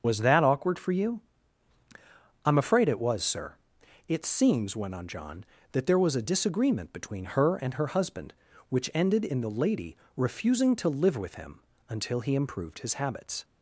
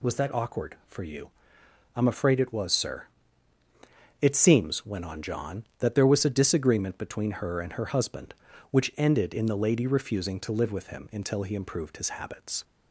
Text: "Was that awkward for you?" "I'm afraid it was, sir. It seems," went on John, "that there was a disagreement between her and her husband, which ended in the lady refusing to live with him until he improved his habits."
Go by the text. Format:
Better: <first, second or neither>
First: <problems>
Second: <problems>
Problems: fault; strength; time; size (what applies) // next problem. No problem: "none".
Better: second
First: loses the start of "Was"; at 0.0 s; 35 ms // starts louder than the rest; until 1.0 s; 6.5 dB // pauses between "lady" and "refusing"; slight; at 9.9 s; 0.20 s long // pauses between "him" and "until"; slight; at 11.6 s; 0.26 s long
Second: none